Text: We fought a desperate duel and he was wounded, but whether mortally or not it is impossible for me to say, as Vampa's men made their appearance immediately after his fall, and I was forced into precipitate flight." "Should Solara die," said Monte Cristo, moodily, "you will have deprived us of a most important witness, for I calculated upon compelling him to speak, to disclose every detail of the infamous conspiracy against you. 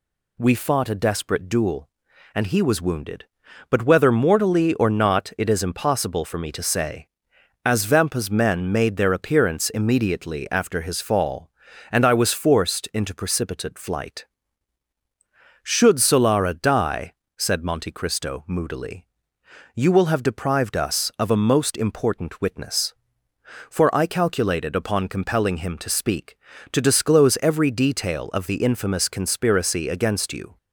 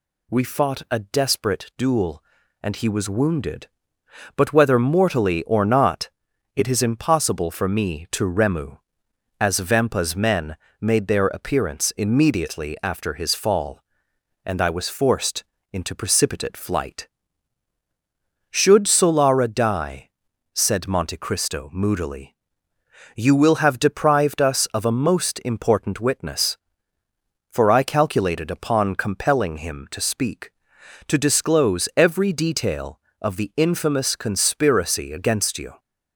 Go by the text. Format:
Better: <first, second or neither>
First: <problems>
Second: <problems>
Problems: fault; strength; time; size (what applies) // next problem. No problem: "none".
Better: first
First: none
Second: pauses between "not" and "it"; noticeable; at 6.0 s; 0.46 s long // says "remu" for "say"; at 8.2 s // pauses between "men" and "made"; slight; at 10.5 s; 0.24 s long // pauses between "forced" and "into"; slight; at 15.4 s; 0.26 s long